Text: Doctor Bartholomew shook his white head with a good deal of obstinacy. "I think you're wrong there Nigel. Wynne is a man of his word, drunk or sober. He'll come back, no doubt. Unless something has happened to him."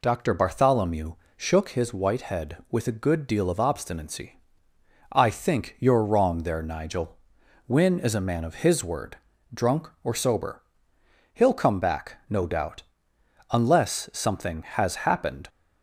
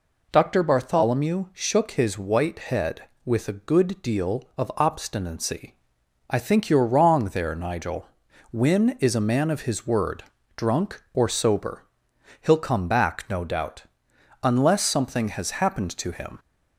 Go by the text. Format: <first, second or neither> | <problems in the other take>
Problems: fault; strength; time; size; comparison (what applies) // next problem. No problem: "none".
second | pauses between "Bartholomew" and "shook"; slight; at 1.1 s; 0.22 s long // stops before "to him"; at 15.4 s